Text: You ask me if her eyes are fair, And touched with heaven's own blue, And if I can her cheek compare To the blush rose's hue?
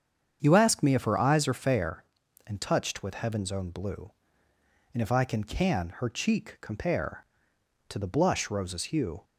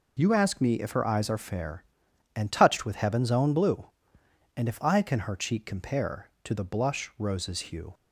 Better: second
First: starts louder than the rest; strong; until 1.4 s; 7.5 dB // says "can" twice; at 5.4 s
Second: none

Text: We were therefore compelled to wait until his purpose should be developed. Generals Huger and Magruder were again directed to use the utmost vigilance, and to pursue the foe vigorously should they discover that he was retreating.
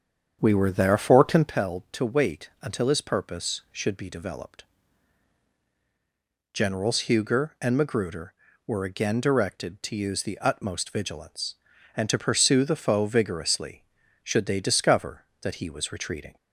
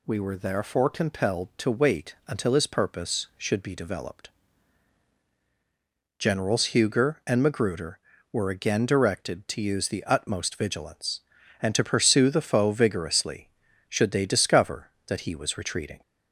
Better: second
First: starts louder than the rest; strong; until 1.5 s; 8 dB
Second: none

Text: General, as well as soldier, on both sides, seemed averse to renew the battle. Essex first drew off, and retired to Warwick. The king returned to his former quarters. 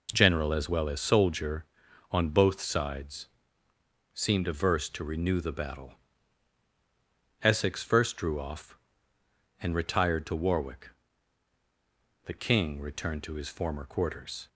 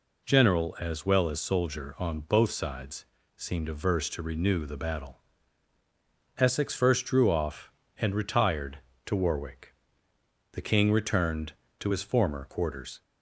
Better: neither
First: none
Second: none

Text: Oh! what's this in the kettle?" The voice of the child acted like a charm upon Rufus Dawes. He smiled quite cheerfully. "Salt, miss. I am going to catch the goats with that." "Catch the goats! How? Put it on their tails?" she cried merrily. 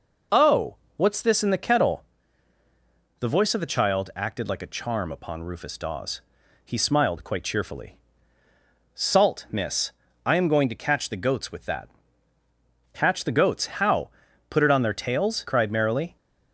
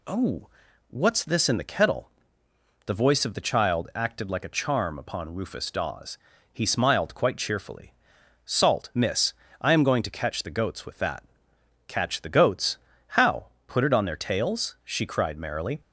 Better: second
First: skips "she"; at 15.4 s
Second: none

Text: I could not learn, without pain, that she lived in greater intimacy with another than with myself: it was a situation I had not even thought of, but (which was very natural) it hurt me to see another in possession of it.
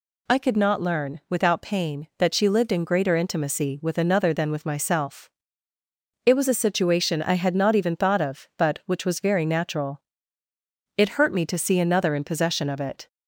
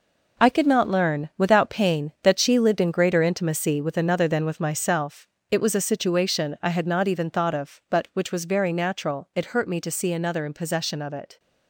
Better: first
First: none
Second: gets quieter; strong; throughout; 9 dB

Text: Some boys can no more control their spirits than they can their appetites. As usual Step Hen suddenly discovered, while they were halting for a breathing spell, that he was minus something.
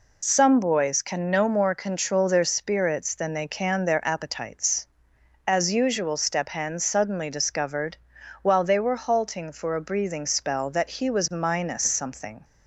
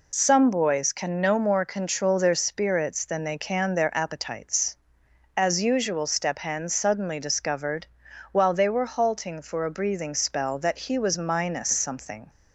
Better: neither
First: none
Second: none

